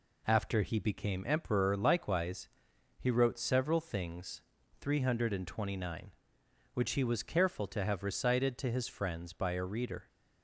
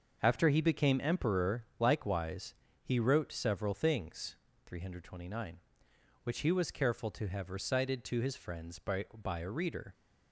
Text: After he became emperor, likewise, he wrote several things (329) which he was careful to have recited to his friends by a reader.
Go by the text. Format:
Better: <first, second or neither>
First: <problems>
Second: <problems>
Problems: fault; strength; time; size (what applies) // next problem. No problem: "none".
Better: first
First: none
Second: starts louder than the rest; until 1.2 s; 6.5 dB // says "by" twice; at 9.1 s